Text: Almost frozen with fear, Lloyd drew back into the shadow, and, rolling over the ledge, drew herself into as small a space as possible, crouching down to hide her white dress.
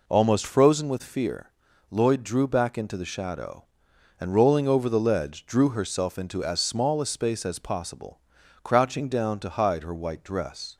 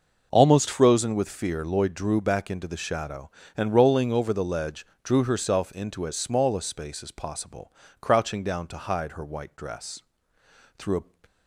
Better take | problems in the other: first | goes on to say "Through a"; slight; from 10.7 s on; 0.30 s long

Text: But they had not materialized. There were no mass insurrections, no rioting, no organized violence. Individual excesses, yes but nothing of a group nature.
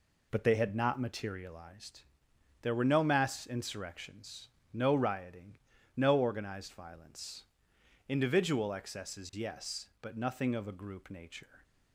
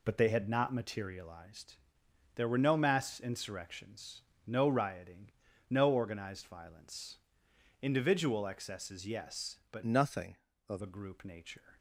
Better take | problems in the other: first | changes voice from "nothing" to "of"; from 9.8 to 10.8 s; 1.0 s long

